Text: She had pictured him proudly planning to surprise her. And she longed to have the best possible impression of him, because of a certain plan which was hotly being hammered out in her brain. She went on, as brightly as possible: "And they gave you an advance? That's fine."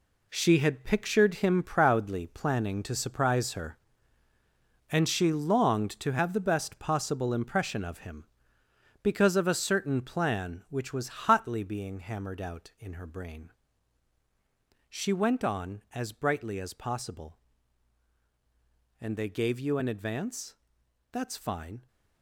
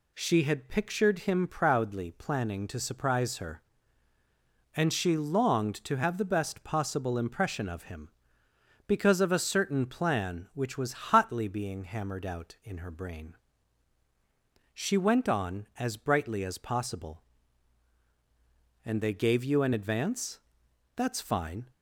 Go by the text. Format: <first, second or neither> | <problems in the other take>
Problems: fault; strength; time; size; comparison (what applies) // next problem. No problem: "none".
second | gets quieter; strong; throughout; 10 dB